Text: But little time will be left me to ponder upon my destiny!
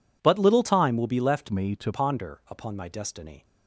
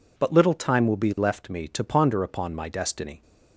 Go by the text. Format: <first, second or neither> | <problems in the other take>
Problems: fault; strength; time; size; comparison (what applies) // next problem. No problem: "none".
second | changes voice from "me" to "to"; from 1.4 to 1.9 s; 0.5 s long